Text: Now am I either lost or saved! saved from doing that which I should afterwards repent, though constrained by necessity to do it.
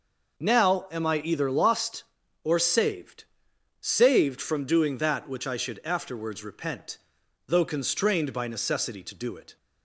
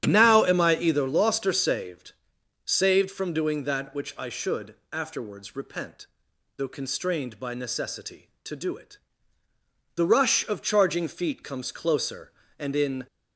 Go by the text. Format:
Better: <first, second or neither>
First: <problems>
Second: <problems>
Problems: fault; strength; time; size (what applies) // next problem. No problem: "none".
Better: first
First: none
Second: starts louder than the rest; strong; until 1.0 s; 10 dB // pauses between "should" and "afterwards"; slight; at 4.7 s; 0.16 s long // goes on to say "The rush of charging feet comes closer and in"; strong; from 9.9 s on; 3.1 s long